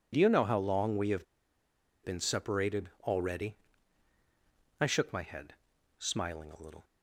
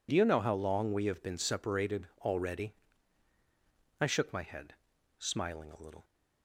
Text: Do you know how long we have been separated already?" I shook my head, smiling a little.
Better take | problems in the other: second | pauses between "have" and "been"; noticeable; at 1.2 s; 0.78 s long

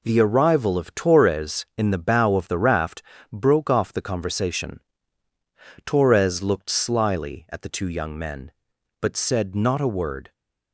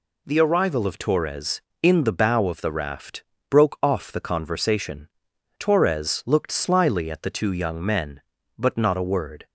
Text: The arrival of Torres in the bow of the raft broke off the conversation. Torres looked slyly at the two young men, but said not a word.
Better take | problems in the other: first | pauses between "raft" and "broke"; slight; at 3.2 s; 0.26 s long; slight in the first // skips "said"; at 8.7 s

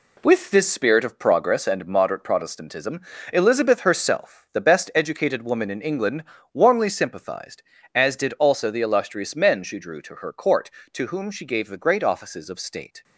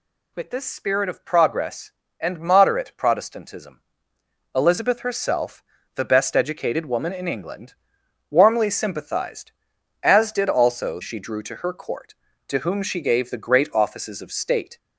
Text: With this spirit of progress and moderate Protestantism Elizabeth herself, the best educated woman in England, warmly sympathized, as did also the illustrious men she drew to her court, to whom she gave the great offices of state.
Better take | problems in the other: first | pauses between "Protestantism" and "Elizabeth"; noticeable; at 3.8 s; 0.74 s long; slight in the first // skips "the illustrious men"; at 11.0 s

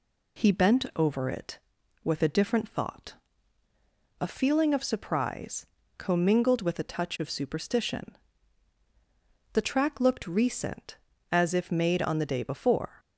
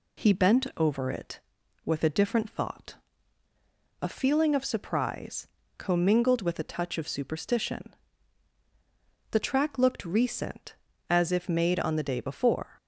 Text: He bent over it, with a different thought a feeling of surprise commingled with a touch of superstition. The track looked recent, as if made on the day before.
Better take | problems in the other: neither | pauses between "thought" and "a"; the same in both // pauses between "surprise" and "commingled"; slight; the same in both

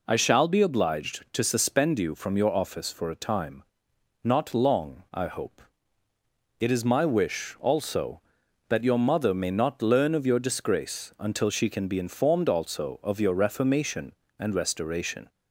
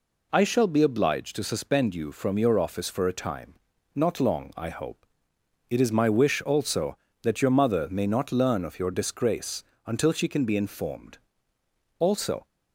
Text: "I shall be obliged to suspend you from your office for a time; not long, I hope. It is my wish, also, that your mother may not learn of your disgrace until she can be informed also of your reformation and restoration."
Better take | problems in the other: first | pauses between "disgrace" and "until"; slight; at 9.6 s; 0.22 s long // pauses between "informed" and "also"; noticeable; at 11.1 s; 0.78 s long // stops before "of your reformation and restoration"; at 12.4 s

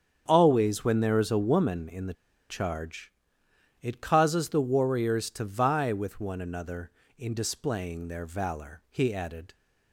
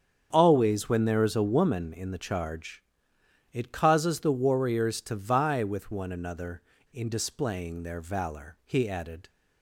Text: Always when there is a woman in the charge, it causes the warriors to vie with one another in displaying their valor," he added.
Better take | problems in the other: second | starts louder than the rest; strong; until 1.2 s; 8 dB; strong in the second // pauses between "the" and "charge"; at 2.1 s; 0.36 s long

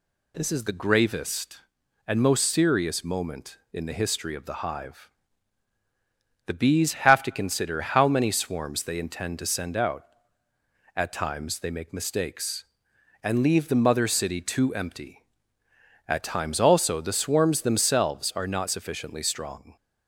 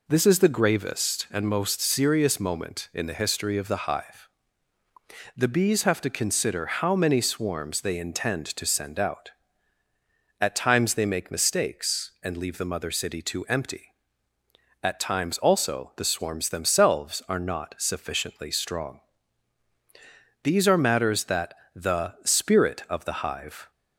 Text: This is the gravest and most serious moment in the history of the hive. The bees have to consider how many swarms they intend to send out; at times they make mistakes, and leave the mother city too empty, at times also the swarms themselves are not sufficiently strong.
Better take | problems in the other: first | goes on to say "These are matters that the spirit of the hive"; strong; from 20.4 s on; 3.2 s long

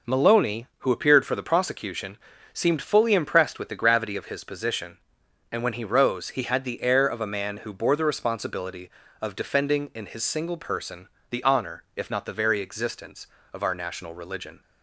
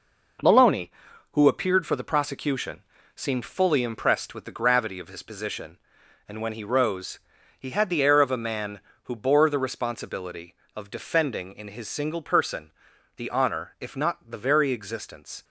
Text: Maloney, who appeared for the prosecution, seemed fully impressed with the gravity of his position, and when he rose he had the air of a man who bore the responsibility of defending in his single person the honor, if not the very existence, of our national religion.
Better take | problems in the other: first | pauses between "rose" and "he"; at 7.1 s; 0.40 s long // pauses between "person" and "the"; noticeable; at 12.6 s; 0.48 s long; slight in the first // stops before "of our national religion"; at 15.4 s

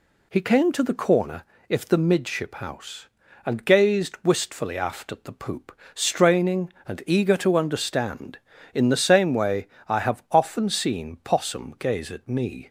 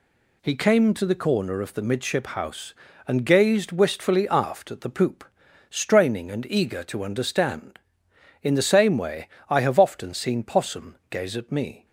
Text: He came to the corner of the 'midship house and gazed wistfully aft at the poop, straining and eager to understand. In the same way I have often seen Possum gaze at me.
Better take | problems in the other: second | says "if" for "of"; at 1.6 s // pauses between "way" and "I"; slight; at 9.6 s; 0.20 s long; slight in the second

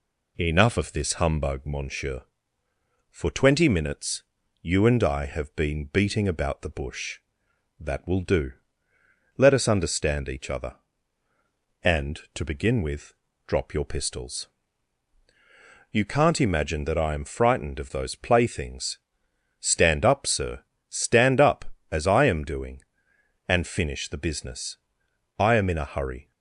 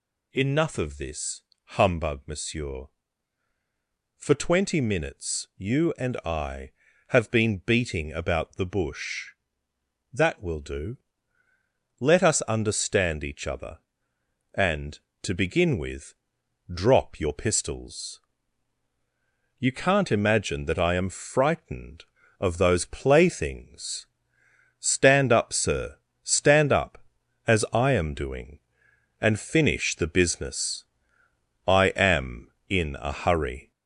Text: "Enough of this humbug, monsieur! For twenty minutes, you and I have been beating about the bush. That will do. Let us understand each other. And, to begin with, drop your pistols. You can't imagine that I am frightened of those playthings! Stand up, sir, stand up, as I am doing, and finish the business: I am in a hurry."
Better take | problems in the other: first | gets louder; throughout; 3.5 dB // pauses between "this" and "humbug"; slight; at 1.4 s; 0.34 s long

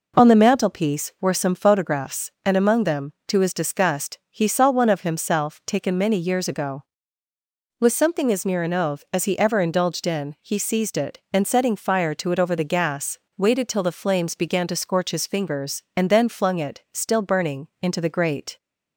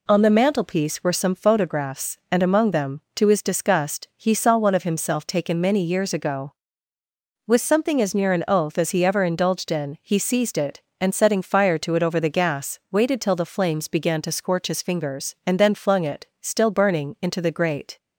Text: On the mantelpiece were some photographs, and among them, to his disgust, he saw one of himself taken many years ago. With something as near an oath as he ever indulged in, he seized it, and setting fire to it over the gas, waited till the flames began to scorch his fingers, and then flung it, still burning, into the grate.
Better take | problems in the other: neither | none

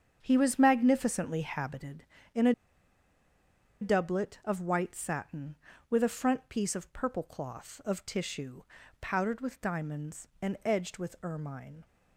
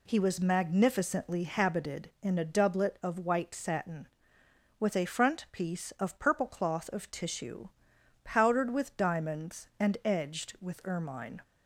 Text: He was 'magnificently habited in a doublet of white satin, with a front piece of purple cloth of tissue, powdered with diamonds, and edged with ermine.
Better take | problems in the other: second | starts louder than the rest; strong; until 1.2 s; 7.5 dB // pauses between "a" and "doublet"; strong; at 2.5 s; 1.2 s long

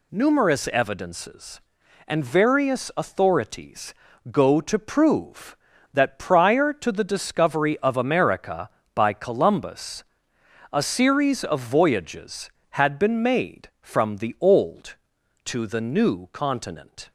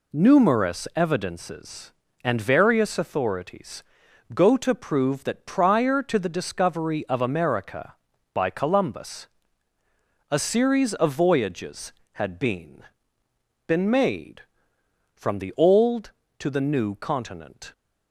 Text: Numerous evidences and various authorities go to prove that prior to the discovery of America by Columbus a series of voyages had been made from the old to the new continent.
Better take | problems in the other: first | pauses between "authorities" and "go"; noticeable; at 3.8 s; 0.54 s long; also in the first // pauses between "Columbus" and "a"; at 9.2 s; 1.0 s long; noticeable in the first // says "been" twice; at 13.6 s

